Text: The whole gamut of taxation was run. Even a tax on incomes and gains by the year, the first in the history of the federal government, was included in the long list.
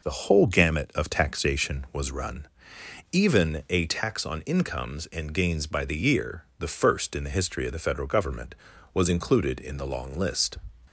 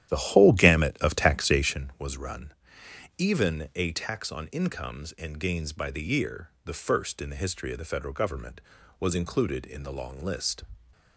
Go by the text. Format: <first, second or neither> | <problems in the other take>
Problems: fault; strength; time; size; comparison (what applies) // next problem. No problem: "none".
first | starts louder than the rest; strong; until 1.8 s; 11.5 dB